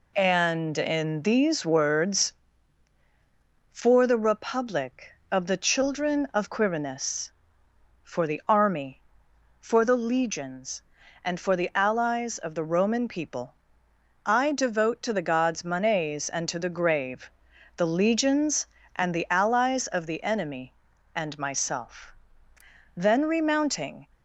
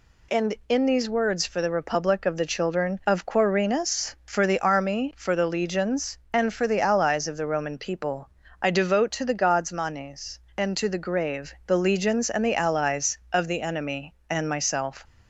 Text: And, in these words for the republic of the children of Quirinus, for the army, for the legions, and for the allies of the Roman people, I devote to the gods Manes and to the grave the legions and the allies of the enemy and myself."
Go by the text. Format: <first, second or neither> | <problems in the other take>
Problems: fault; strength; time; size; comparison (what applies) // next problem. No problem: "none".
second | pauses between "grave" and "the"; noticeable; at 17.3 s; 0.46 s long // goes on to say "Then remounting"; noticeable; from 22.9 s on; 1.1 s long